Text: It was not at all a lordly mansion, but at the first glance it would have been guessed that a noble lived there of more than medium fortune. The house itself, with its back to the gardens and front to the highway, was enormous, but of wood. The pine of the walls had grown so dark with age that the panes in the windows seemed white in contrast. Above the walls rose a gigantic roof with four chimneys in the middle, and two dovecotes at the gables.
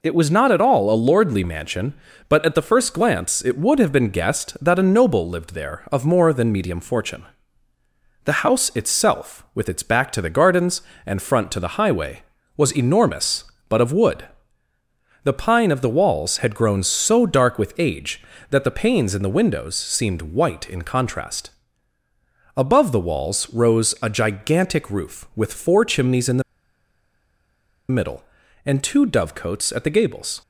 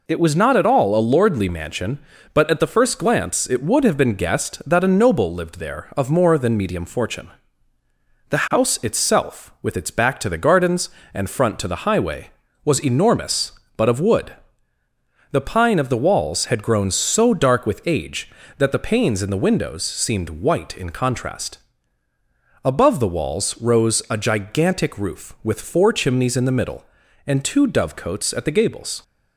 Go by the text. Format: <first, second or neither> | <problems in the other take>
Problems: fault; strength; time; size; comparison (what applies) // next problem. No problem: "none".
second | pauses between "the" and "middle"; strong; at 26.4 s; 1.4 s long